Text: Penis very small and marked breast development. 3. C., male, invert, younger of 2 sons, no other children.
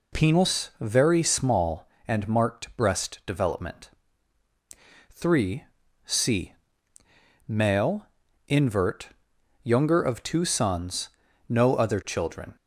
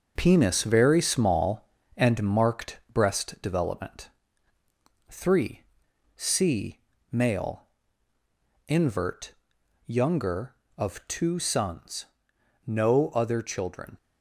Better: first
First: none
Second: gets quieter; throughout; 6 dB

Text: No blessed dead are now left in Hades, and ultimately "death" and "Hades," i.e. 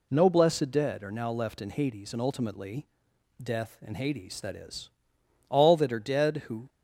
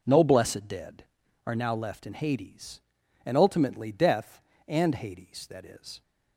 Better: second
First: pauses between "ultimately" and "death"; noticeable; at 2.8 s; 0.58 s long // goes on to say "all that are dead who"; noticeable; from 5.4 s on; 1.2 s long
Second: none

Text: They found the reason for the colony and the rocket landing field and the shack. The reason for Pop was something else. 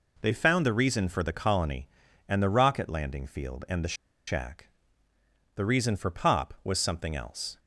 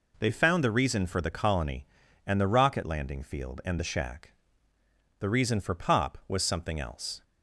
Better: second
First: pauses between "the" and "shack"; slight; at 3.9 s; 0.34 s long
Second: none

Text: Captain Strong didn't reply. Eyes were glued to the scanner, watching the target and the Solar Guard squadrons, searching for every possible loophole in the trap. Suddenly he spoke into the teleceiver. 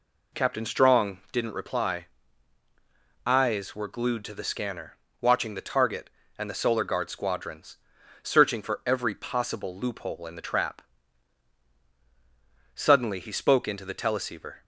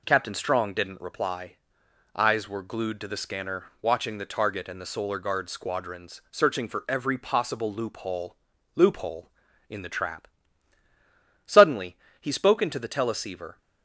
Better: first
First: none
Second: says "loophole" twice; at 8.7 s // pauses between "Suddenly" and "he"; slight; at 11.9 s; 0.24 s long

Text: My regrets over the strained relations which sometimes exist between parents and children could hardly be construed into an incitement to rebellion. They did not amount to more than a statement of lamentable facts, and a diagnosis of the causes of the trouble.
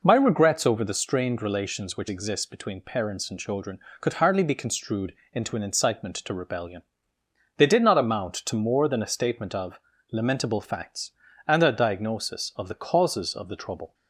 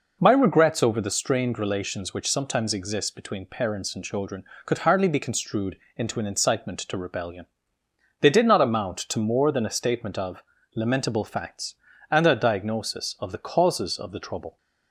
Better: second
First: skips "sometimes"; at 2.0 s // pauses between "construed" and "into"; slight; at 5.1 s; 0.18 s long // pauses between "of" and "lamentable"; slight; at 9.7 s; 0.34 s long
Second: pauses between "construed" and "into"; slight; at 5.7 s; 0.18 s long // pauses between "of" and "lamentable"; slight; at 10.4 s; 0.34 s long

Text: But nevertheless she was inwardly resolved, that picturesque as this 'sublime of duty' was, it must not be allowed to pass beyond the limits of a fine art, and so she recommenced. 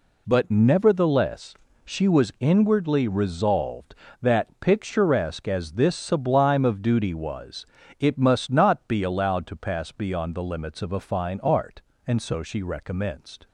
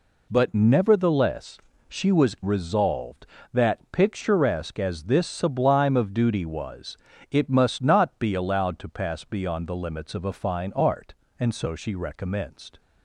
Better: first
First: pauses between "nevertheless" and "she"; slight; at 1.5 s; 0.28 s long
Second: pauses between "nevertheless" and "she"; slight; at 1.5 s; 0.28 s long // skips "inwardly"; at 2.3 s

